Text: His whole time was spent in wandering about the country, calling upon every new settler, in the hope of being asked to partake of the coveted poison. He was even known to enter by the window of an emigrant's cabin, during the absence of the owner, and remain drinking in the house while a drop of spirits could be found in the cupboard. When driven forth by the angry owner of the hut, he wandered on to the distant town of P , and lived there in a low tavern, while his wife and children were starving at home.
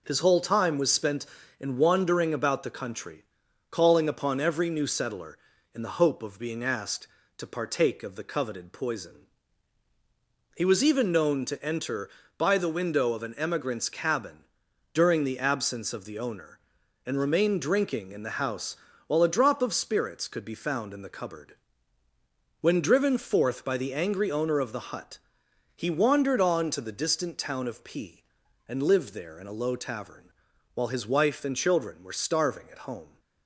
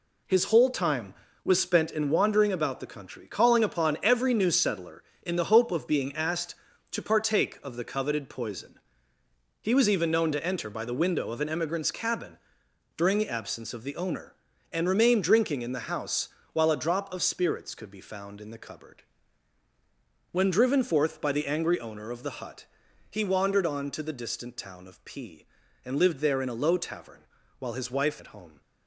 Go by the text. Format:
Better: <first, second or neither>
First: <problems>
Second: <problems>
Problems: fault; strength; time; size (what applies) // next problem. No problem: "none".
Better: first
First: pauses between "house" and "while"; slight; at 18.7 s; 0.32 s long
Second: pauses between "house" and "while"; slight; at 16.2 s; 0.26 s long // skips "and children were starving"; at 28.1 s